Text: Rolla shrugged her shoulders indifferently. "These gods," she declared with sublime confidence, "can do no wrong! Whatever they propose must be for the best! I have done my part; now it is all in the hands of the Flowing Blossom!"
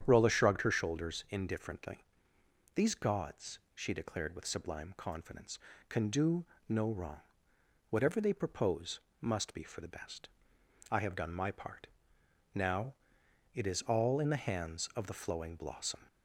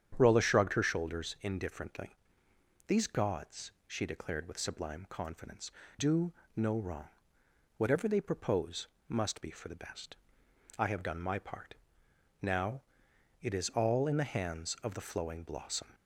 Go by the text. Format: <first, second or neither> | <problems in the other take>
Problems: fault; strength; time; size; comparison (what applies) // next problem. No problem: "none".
first | starts louder than the rest; strong; until 1.1 s; 8.5 dB; strong in the first // skips "can"; at 5.8 s // pauses between "do" and "no"; slight; at 6.3 s; 0.20 s long; slight in the first // pauses between "propose" and "must"; slight; at 8.8 s; 0.22 s long; slight in the first // pauses between "now" and "it"; noticeable; at 12.8 s; 0.58 s long; noticeable in the first